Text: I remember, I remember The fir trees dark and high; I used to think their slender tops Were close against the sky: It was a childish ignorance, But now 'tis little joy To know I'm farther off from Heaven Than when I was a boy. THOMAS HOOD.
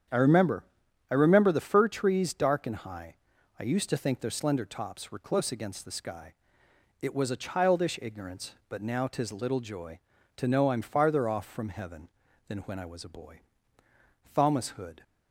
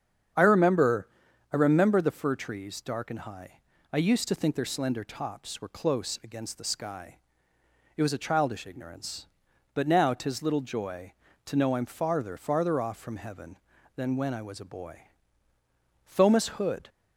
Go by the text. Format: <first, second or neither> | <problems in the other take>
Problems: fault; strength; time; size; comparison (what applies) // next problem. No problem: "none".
first | starts louder than the rest; strong; until 1.8 s; 8 dB; strong in the first // says "farther" twice; at 12.3 s